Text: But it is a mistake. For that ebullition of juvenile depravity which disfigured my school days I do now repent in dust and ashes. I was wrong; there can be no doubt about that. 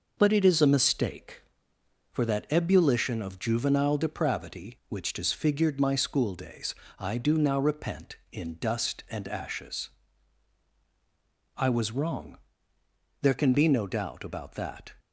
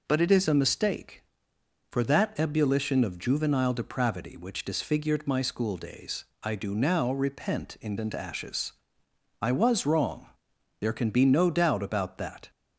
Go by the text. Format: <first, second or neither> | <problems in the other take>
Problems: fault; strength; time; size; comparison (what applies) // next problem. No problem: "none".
first | pauses between "days" and "I"; slight; at 6.2 s; 0.18 s long; slight in the first // skips "dust"; at 7.9 s